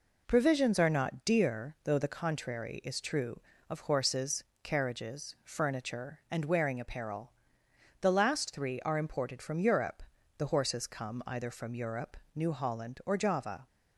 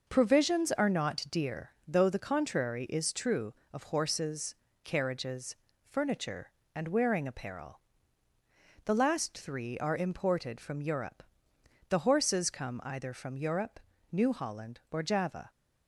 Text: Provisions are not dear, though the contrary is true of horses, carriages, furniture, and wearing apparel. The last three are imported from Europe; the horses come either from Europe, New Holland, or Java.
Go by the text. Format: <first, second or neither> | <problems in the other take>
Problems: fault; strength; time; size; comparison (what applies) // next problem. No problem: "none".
neither | none